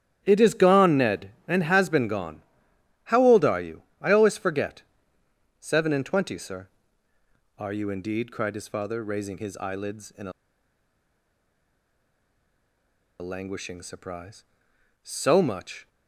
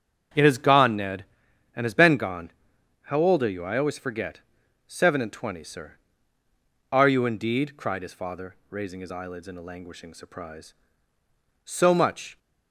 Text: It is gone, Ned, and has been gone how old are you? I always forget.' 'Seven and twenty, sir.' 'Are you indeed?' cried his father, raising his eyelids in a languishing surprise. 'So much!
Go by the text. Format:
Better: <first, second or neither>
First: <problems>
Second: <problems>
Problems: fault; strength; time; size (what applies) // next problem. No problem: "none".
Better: second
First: starts louder than the rest; strong; until 1.2 s; 11 dB // pauses between "gone" and "how"; noticeable; at 2.4 s; 0.66 s long // pauses between "a" and "languishing"; strong; at 10.3 s; 2.8 s long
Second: starts louder than the rest; strong; until 1.8 s; 7.5 dB // pauses between "gone" and "how"; noticeable; at 2.5 s; 0.52 s long